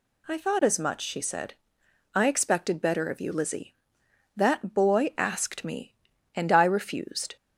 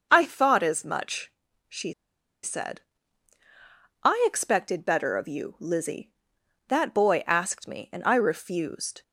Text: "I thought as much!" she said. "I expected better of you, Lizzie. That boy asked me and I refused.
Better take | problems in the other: first | starts louder than the rest; until 1.1 s; 6 dB // pauses between "she" and "said"; noticeable; at 1.9 s; 0.52 s long

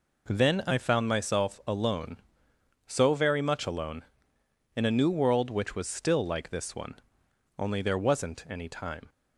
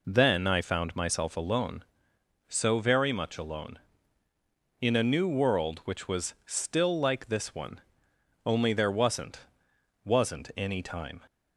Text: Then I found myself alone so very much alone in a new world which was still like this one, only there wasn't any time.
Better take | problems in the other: first | says "wasn't" twice; at 10.0 s

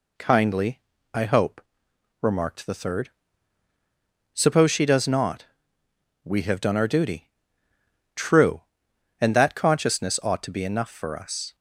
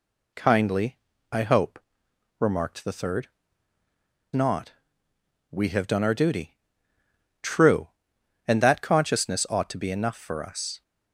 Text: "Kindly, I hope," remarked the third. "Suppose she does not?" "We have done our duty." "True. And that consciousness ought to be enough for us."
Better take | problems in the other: first | skips "Suppose she does"; at 3.8 s

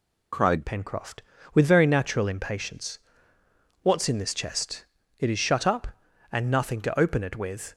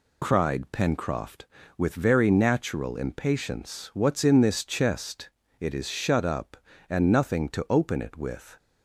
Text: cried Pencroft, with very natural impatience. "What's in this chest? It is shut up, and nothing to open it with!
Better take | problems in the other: second | changes voice at "Pencroft"; from 0.6 s on; 7.1 s long

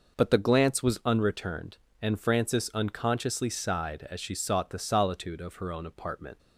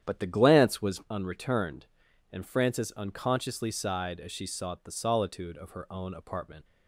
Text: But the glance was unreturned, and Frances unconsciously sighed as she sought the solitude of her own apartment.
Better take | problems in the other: first | starts louder than the rest; strong; until 1.1 s; 9.5 dB

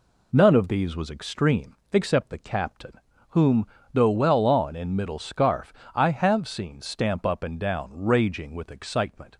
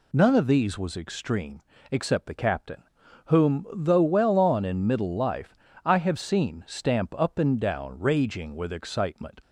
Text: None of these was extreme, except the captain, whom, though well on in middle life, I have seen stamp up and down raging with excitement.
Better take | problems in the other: second | says "scarf" for "life"; at 5.1 s

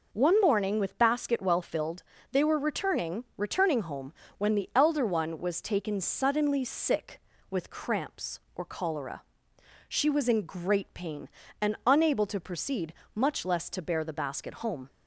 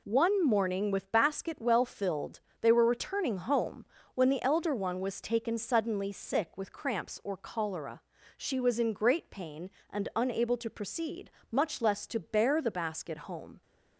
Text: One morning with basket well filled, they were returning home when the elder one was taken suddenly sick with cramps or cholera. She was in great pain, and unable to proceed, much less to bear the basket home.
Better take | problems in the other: second | says "returning" twice; at 3.3 s // pauses between "home" and "when"; slight; at 4.1 s; 0.26 s long; slight in the second

